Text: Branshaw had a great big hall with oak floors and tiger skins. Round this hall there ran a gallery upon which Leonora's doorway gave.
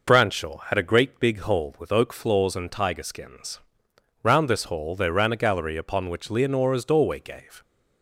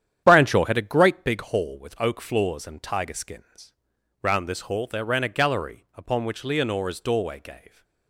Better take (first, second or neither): first